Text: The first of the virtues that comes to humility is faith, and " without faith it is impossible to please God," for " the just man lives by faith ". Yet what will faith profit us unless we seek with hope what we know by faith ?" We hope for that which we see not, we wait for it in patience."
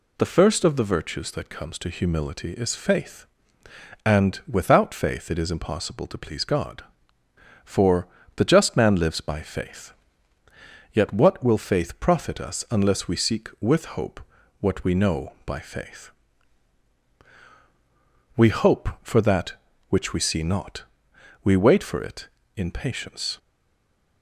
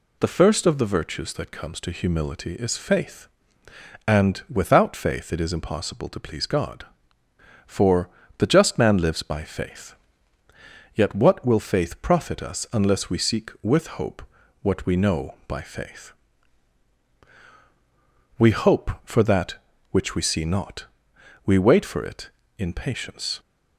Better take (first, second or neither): second